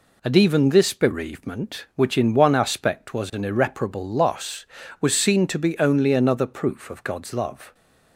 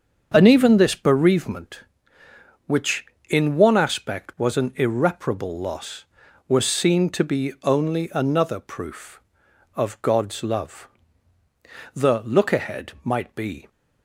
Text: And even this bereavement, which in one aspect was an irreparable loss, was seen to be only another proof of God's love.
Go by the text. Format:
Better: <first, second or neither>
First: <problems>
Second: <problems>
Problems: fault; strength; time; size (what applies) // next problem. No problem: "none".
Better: first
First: none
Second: starts louder than the rest; until 1.3 s; 6.5 dB // goes on to say "The look ahead might be"; strong; from 11.9 s on; 1.7 s long